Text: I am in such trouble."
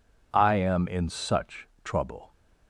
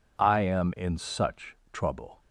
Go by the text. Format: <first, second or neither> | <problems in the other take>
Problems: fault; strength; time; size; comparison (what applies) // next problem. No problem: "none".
neither | pauses between "such" and "trouble"; slight; the same in both